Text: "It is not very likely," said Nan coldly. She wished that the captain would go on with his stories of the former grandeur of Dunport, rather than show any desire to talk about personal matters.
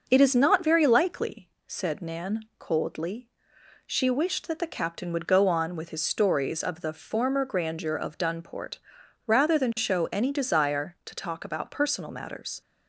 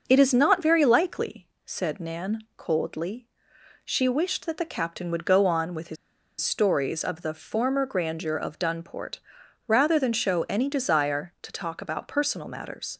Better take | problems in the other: first | pauses between "his" and "stories"; at 5.9 s; 0.45 s long

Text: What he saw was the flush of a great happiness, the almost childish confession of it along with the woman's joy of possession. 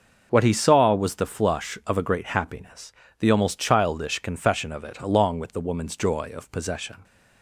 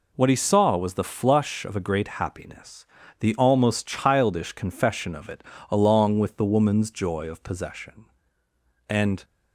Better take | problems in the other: first | pauses between "it" and "along"; slight; at 5.4 s; 0.28 s long // goes on to say "And"; slight; from 8.8 s on; 0.36 s long

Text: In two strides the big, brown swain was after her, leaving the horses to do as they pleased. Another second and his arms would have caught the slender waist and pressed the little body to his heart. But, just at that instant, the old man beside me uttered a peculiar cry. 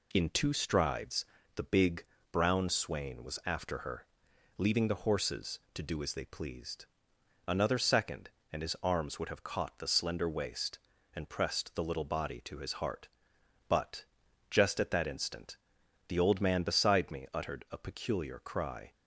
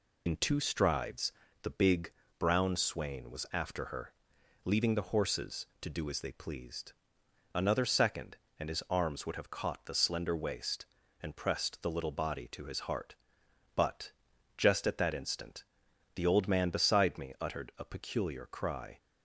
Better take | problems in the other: first | loses the start of "In"; at 0.2 s; 80 ms // pauses between "strides" and "the"; slight; at 1.3 s; 0.32 s long; slight in the first

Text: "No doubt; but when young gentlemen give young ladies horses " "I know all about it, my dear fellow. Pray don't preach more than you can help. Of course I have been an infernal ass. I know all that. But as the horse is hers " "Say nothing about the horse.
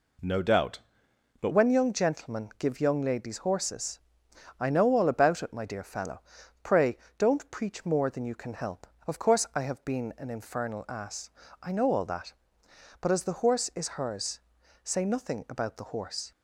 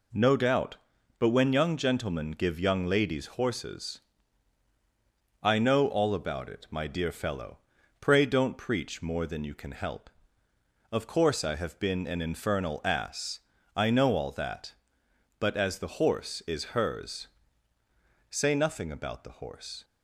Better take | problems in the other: second | changes voice at "when"; from 1.5 s on; 14.8 s long // pauses between "Pray" and "don't"; slight; at 6.9 s; 0.20 s long

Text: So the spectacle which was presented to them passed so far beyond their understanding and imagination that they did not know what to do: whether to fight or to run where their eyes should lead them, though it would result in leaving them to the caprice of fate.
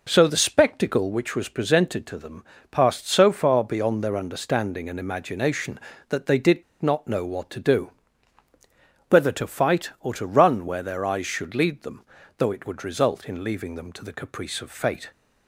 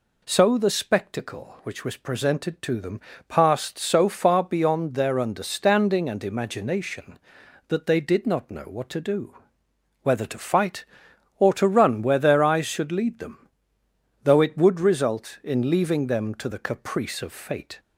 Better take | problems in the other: second | pauses between "them" and "passed"; slight; at 2.4 s; 0.26 s long; slight in the second // pauses between "did" and "not"; slight; at 6.6 s; 0.19 s long

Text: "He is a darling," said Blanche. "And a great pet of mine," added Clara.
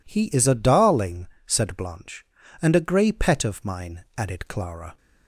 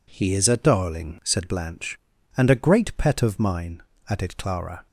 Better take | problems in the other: second | says "grey" for "great"; at 2.8 s

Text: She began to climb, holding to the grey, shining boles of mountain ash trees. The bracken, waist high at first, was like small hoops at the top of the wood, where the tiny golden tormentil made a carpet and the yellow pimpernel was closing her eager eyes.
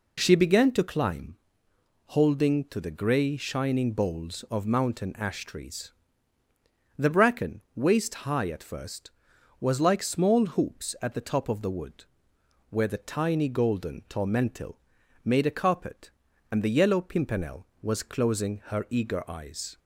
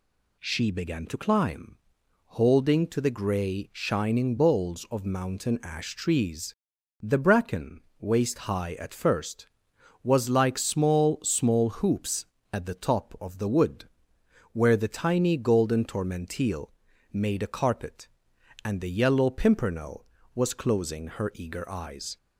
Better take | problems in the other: first | says "small" twice; at 11.2 s // pauses between "tormentil" and "made"; at 16.7 s; 0.40 s long; also in the first

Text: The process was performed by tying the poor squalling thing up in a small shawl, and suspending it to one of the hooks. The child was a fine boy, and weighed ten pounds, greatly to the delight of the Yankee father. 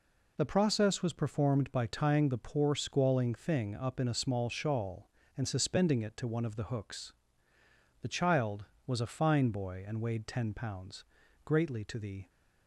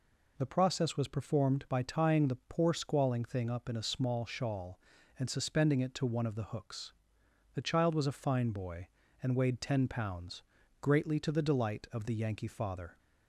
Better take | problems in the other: second | stops before "delight of the Yankee father"; at 12.2 s

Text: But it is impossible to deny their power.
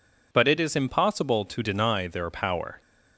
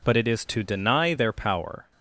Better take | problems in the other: first | skips "impossible"; at 0.4 s

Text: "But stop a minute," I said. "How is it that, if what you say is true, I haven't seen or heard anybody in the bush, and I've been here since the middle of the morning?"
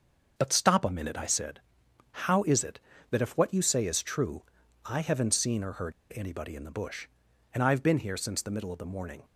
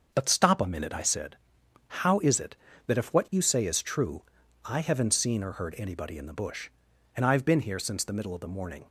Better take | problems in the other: second | starts louder than the rest; until 1.3 s; 6.5 dB; also in the second // pauses between "heard" and "anybody"; slight; at 5.9 s; 0.22 s long

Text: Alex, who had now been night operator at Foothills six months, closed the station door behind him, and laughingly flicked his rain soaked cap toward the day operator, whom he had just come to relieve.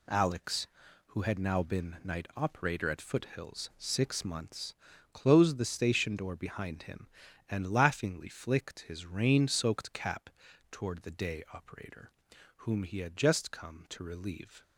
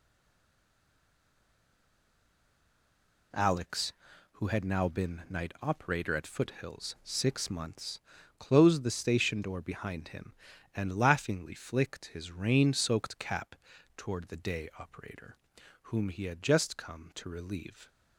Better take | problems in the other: first | stays silent before the first word; strong; until 3.3 s; 3.3 s long // pauses between "cap" and "toward"; at 13.5 s; 0.40 s long; also in the first

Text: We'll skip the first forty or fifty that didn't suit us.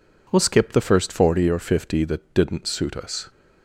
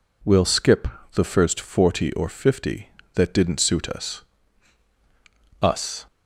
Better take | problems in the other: first | pauses between "skip" and "the"; slight; at 0.8 s; 0.28 s long // says "us" twice; at 5.6 s

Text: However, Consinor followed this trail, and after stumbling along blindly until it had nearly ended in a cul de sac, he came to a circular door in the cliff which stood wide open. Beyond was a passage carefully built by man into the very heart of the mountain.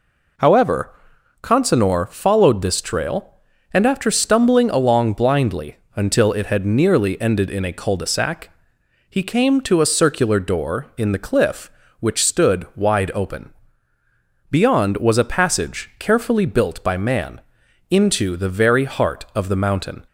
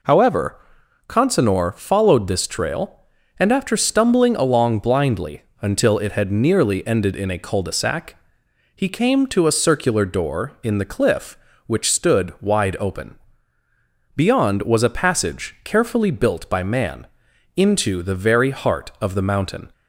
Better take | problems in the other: neither | pauses between "blindly" and "until"; slight; the same in both // pauses between "man" and "into"; noticeable; the same in both

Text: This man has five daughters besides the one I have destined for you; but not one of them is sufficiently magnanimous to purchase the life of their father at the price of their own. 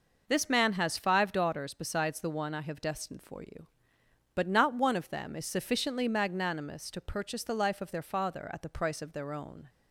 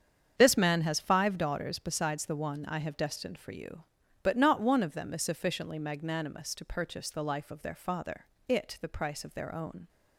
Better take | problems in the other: first | starts louder than the rest; strong; until 1.4 s; 7.5 dB // says "it" for "at"; at 8.4 s

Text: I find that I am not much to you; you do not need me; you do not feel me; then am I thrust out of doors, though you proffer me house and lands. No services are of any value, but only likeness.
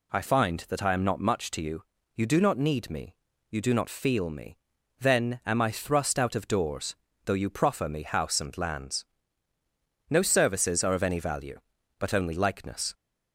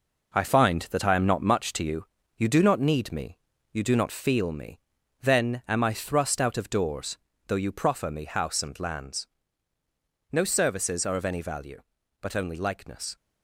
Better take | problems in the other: first | gets quieter; throughout; 7 dB

